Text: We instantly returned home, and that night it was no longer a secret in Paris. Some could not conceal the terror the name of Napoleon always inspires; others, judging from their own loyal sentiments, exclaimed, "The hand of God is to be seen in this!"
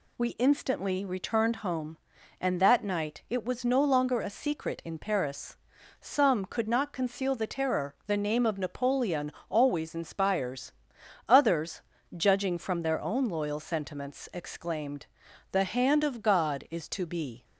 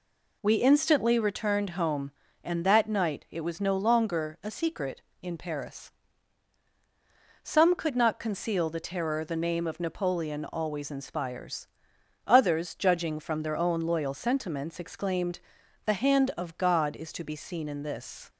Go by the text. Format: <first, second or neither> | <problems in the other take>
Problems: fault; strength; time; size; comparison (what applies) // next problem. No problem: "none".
second | pauses between "Napoleon" and "always"; slight; at 9.2 s; 0.20 s long // stops before "seen in this"; at 17.4 s